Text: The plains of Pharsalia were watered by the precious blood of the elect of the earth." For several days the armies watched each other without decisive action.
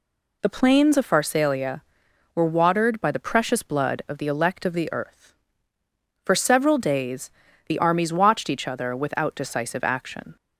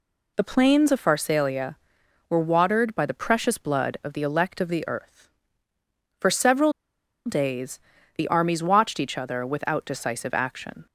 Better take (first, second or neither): first